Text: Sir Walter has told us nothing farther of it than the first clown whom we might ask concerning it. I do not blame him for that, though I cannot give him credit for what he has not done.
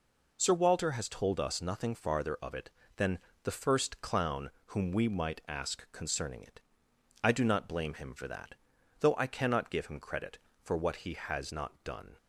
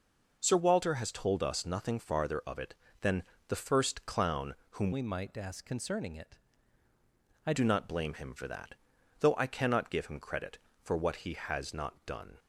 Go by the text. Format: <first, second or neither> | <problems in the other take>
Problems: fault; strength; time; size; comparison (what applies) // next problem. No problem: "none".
first | pauses between "than" and "the"; slight; at 3.2 s; 0.26 s long; slight in the first // pauses between "clown" and "whom"; slight; at 4.5 s; 0.18 s long; slight in the first // changes voice from "we" to "I"; from 4.9 to 7.5 s; 2.6 s long